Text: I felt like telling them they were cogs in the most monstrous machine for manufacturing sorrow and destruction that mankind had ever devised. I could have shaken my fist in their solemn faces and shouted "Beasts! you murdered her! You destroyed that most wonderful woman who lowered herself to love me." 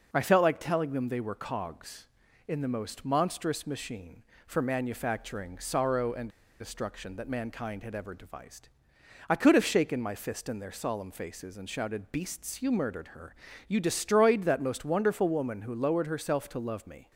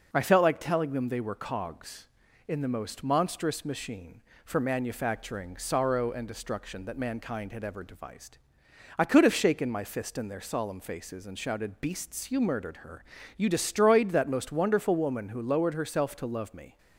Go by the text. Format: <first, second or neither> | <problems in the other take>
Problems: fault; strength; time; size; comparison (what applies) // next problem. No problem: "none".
second | pauses between "and" and "destruction"; slight; at 6.2 s; 0.31 s long